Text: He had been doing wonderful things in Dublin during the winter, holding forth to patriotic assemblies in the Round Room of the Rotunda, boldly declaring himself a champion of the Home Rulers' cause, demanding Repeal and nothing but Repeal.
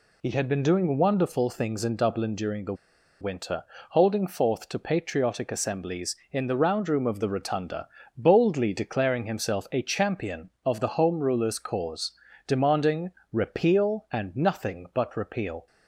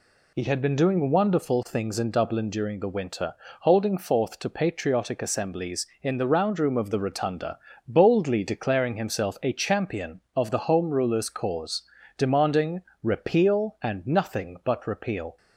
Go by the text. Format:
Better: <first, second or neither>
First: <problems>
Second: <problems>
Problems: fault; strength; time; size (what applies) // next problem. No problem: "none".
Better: second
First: pauses between "the" and "winter"; noticeable; at 2.7 s; 0.46 s long // pauses between "demanding" and "Repeal"; slight; at 13.1 s; 0.20 s long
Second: pauses between "demanding" and "Repeal"; slight; at 12.8 s; 0.20 s long